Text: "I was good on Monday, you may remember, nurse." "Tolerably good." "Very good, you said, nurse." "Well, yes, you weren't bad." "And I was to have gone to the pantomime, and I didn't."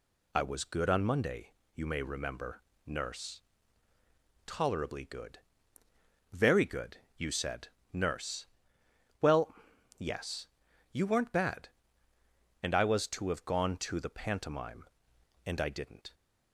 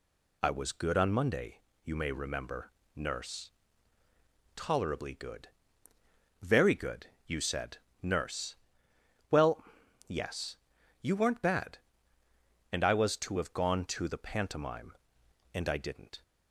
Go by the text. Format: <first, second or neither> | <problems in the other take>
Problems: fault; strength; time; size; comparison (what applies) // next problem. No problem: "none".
neither | none